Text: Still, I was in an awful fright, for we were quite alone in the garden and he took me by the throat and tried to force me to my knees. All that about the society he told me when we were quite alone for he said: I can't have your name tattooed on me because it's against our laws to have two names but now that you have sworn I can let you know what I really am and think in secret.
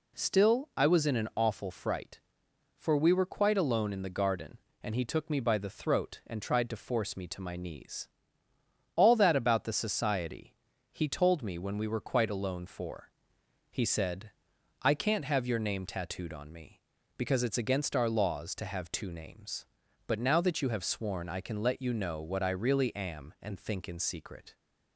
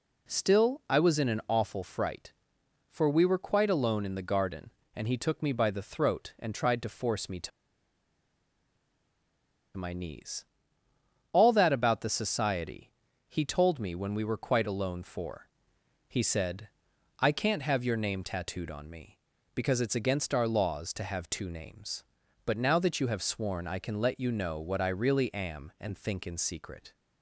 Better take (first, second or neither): first